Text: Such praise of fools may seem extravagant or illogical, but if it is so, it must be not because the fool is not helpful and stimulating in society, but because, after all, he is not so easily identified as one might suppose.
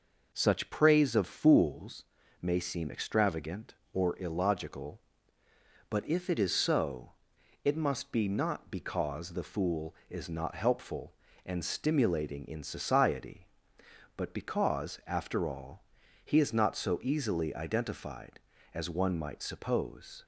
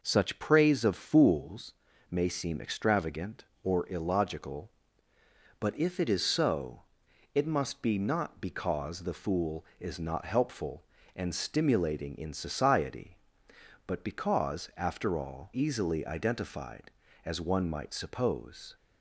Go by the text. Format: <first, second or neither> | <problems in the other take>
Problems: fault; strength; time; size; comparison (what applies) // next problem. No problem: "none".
first | pauses between "fools" and "may"; slight; at 1.7 s; 0.36 s long; slight in the first // skips "he is not so"; at 15.5 s